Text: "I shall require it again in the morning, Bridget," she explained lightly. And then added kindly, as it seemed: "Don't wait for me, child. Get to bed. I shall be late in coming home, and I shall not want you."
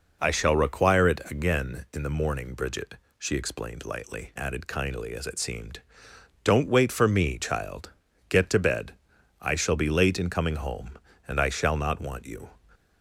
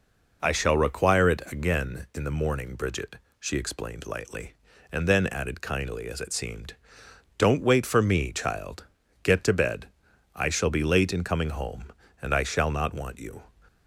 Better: second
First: skips "And then"; at 4.3 s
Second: none

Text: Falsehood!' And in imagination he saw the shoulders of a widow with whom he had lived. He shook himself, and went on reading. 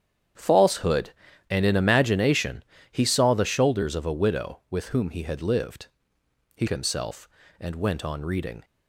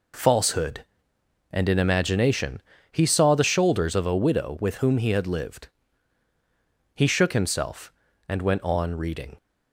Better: second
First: starts louder than the rest; strong; until 1.7 s; 9 dB // pauses between "imagination" and "he"; slight; at 2.6 s; 0.26 s long // skips "shook"; at 6.6 s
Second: pauses between "imagination" and "he"; slight; at 2.6 s; 0.30 s long

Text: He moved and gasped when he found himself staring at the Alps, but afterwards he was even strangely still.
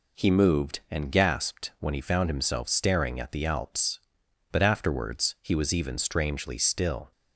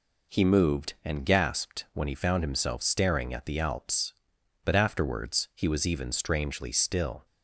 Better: neither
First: none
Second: none

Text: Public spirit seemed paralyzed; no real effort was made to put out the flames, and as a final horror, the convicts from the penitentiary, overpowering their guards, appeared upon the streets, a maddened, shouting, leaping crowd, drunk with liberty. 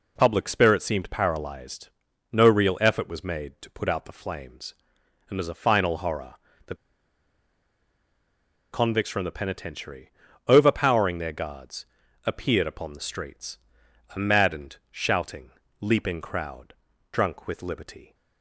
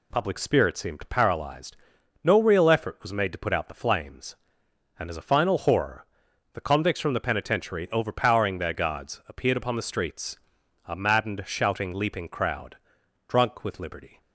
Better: second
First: pauses between "the" and "convicts"; strong; at 6.7 s; 1.9 s long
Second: none

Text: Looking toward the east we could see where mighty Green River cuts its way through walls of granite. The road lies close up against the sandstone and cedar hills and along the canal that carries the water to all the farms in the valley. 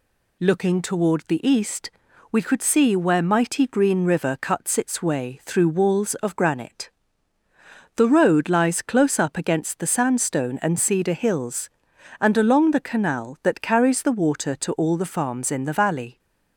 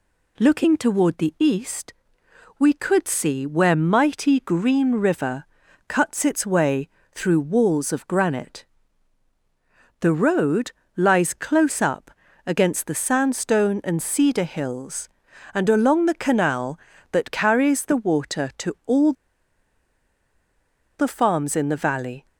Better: first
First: pauses between "east" and "we"; at 1.8 s; 0.40 s long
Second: pauses between "east" and "we"; noticeable; at 1.9 s; 0.66 s long // pauses between "River" and "cuts"; at 5.4 s; 0.42 s long // pauses between "way" and "through"; slight; at 6.8 s; 0.24 s long // pauses between "road" and "lies"; slight; at 10.7 s; 0.24 s long // pauses between "up" and "against"; slight; at 12.1 s; 0.34 s long // pauses between "all" and "the"; strong; at 19.1 s; 1.8 s long

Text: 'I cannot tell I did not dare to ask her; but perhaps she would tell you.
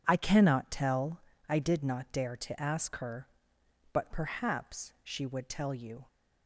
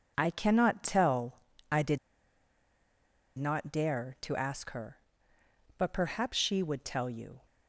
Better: first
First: pauses between "tell" and "I"; slight; at 1.2 s; 0.26 s long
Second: pauses between "tell" and "I"; slight; at 1.4 s; 0.32 s long // pauses between "did" and "not"; strong; at 1.9 s; 1.4 s long

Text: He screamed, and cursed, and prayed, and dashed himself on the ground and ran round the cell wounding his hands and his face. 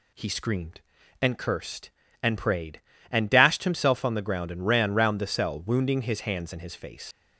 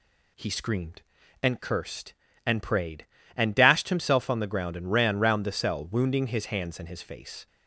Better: second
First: leaves "face" unfinished; at 7.1 s; 80 ms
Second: none

